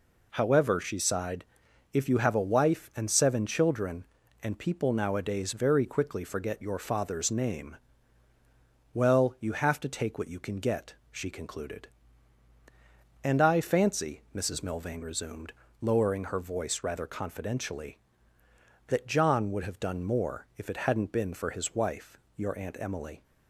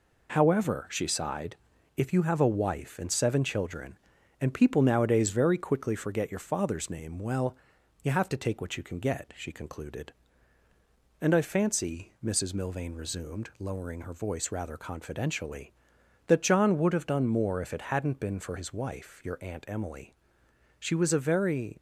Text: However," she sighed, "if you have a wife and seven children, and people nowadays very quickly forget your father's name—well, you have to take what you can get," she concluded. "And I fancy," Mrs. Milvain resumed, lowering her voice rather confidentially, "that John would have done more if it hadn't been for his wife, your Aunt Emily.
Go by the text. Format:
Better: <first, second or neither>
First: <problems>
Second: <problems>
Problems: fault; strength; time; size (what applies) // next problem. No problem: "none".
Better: first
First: none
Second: goes on to say "She was a very"; noticeable; from 20.8 s on; 0.96 s long